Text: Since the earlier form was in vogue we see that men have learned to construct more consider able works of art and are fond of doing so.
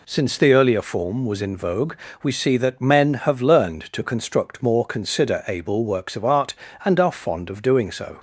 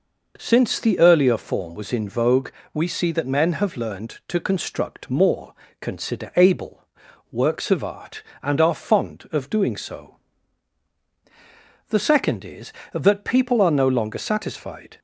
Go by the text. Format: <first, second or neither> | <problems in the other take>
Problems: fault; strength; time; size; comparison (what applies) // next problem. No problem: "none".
first | pauses between "vogue" and "we"; slight; at 2.5 s; 0.24 s long; slight in the first // pauses between "more" and "consider"; slight; at 5.5 s; 0.26 s long // pauses between "able" and "works"; noticeable; at 6.8 s; 0.48 s long // goes on to say "The second is that people are no longer satisfied"; strong; from 11.8 s on; 3.1 s long